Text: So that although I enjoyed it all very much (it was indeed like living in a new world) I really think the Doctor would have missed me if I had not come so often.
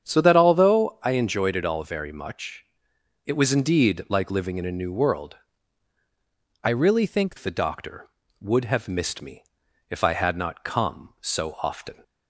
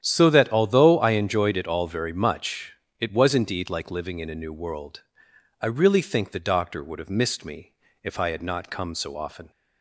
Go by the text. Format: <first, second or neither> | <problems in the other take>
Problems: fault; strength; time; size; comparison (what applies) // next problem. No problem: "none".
second | starts louder than the rest; strong; until 1.0 s; 8 dB; strong in the second // changes voice from "really" to "think"; from 6.6 to 7.3 s; 0.7 s long // pauses between "me" and "if"; at 9.4 s; 0.44 s long; slight in the second